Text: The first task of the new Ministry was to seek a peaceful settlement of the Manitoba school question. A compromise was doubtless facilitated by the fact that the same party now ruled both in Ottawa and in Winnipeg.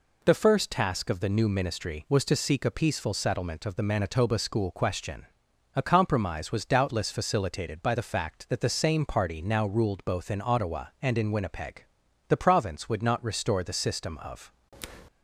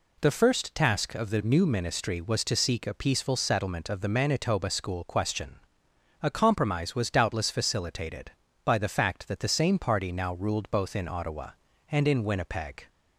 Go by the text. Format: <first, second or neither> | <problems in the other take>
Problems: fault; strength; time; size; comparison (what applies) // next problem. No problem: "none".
second | goes on to say "The province would not restore the system of"; strong; from 12.2 s on; 2.2 s long